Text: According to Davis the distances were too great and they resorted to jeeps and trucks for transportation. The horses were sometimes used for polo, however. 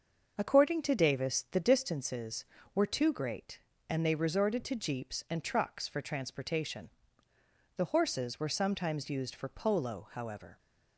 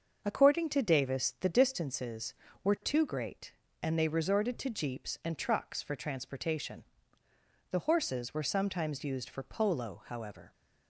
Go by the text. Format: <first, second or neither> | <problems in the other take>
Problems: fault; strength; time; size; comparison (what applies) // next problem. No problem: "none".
neither | starts louder than the rest; the same in both